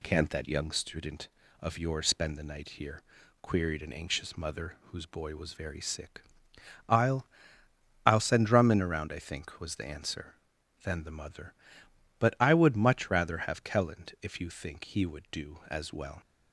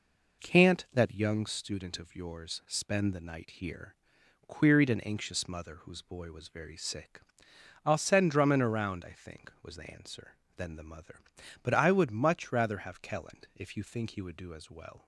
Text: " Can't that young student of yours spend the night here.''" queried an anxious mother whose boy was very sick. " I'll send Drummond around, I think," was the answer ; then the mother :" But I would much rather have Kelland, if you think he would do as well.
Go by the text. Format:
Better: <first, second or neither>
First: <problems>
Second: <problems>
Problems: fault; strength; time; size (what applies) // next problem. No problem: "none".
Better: second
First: says "I'll" twice; at 8.0 s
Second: none